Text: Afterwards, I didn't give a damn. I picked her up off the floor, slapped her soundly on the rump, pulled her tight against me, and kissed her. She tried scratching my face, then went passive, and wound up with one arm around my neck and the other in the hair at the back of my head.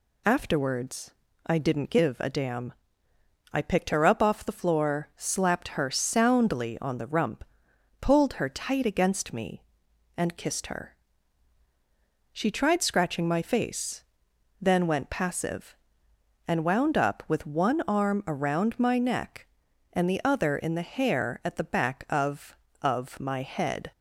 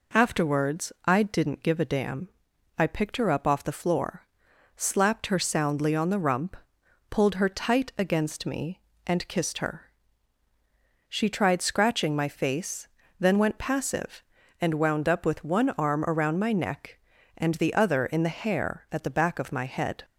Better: second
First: says "of" twice; at 22.8 s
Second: none

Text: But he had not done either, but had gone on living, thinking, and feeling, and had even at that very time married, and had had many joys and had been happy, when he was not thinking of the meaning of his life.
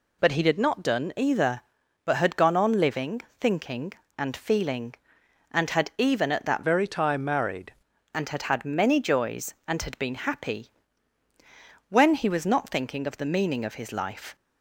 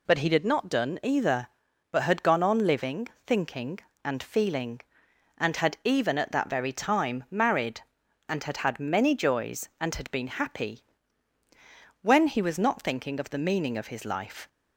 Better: second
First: changes voice from "very" to "married"; from 6.6 to 7.7 s; 1.1 s long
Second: none

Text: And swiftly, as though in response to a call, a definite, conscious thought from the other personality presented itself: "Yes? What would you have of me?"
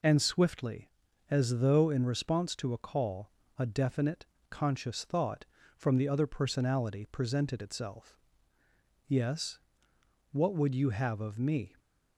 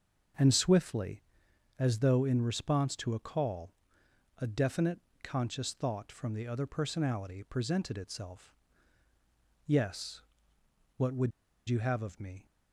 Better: first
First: none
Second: starts louder than the rest; until 1.9 s; 6.5 dB // pauses between "would" and "you"; at 11.3 s; 0.38 s long

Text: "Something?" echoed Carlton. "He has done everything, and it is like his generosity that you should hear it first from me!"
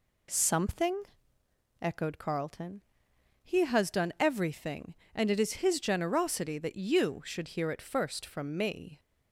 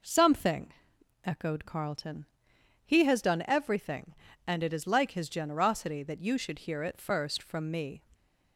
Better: second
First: skips "like"; at 5.6 s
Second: none

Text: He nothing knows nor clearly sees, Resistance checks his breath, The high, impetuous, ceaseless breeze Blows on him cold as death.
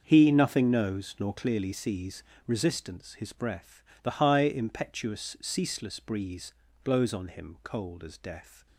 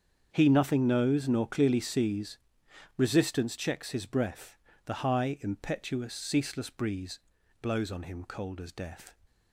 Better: second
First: starts louder than the rest; until 1.0 s; 6.5 dB // skips "checks"; at 3.1 s // pauses between "breeze" and "Blows"; slight; at 6.5 s; 0.32 s long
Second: starts louder than the rest; strong; until 1.3 s; 7 dB // pauses between "breeze" and "Blows"; at 7.2 s; 0.40 s long

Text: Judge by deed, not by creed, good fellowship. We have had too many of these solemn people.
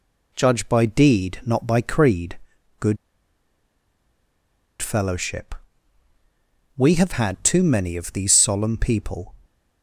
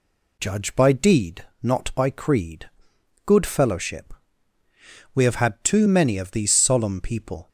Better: second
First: pauses between "good" and "fellowship"; strong; at 2.9 s; 1.8 s long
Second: none

